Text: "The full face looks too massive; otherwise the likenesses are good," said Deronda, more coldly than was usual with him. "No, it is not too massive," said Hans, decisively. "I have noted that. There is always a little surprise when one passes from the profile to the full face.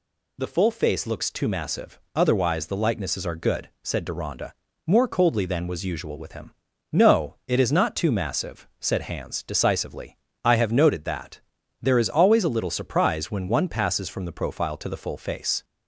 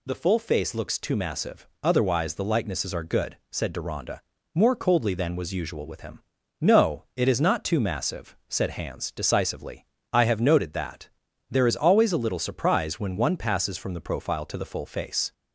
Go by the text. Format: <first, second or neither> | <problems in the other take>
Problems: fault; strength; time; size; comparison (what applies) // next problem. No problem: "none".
neither | none